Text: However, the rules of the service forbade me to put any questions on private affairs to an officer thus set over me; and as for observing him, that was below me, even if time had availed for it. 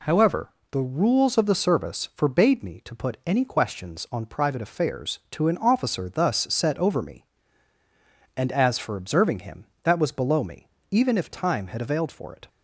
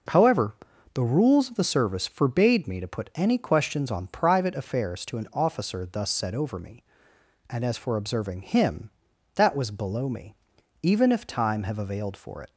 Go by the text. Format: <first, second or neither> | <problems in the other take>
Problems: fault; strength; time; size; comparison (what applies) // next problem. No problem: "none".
first | says "have" for "had"; at 11.6 s